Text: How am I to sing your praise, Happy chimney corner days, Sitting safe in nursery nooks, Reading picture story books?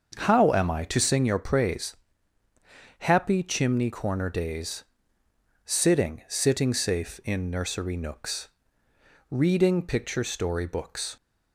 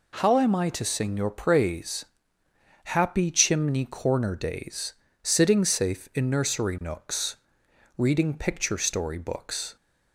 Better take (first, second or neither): second